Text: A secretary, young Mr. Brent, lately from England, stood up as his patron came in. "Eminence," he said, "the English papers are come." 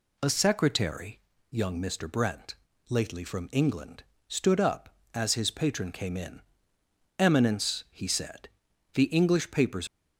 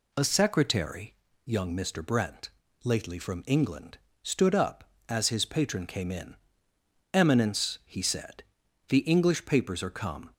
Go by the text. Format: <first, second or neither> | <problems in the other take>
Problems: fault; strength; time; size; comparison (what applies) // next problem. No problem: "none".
second | stops before "are come"; at 9.8 s